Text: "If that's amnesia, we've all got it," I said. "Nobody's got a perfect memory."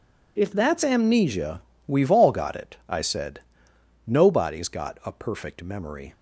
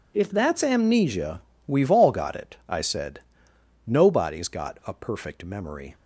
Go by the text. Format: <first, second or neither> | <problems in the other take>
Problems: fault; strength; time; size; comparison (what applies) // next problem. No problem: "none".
neither | none